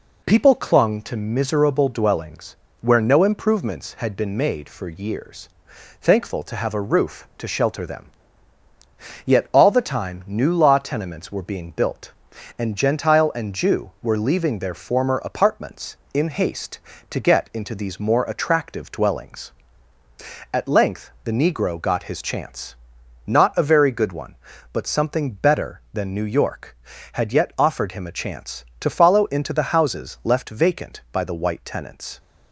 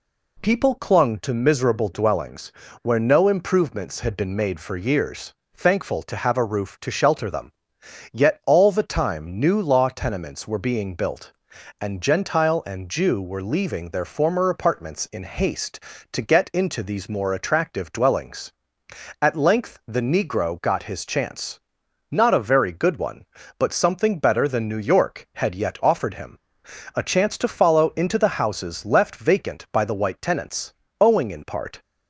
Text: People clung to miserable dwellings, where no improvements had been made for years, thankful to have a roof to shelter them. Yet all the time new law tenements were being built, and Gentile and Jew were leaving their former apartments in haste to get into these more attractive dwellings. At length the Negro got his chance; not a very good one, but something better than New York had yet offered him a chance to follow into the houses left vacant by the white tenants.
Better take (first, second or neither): first